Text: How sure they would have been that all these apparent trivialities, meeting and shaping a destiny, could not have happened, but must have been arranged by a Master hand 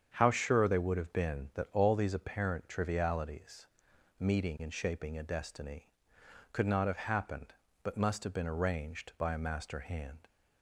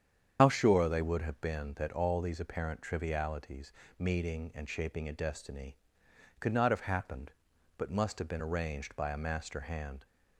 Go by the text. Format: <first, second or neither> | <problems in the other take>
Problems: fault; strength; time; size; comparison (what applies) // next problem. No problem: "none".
first | loses the start of "How"; at 0.3 s; 60 ms // starts louder than the rest; strong; until 1.4 s; 8.5 dB; strong in the first